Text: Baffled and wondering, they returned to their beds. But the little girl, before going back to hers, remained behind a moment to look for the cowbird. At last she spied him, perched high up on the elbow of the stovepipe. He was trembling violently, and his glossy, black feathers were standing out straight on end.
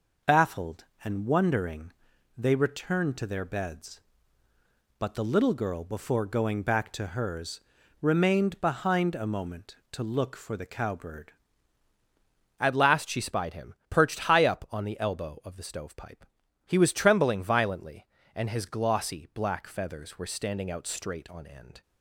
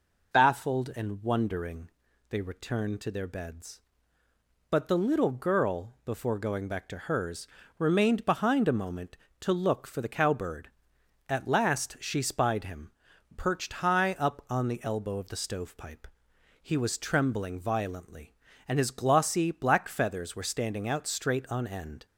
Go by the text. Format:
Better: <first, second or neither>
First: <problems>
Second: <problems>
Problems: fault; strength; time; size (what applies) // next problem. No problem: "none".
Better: second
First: changes voice at "At"; from 12.5 s on; 9.3 s long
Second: none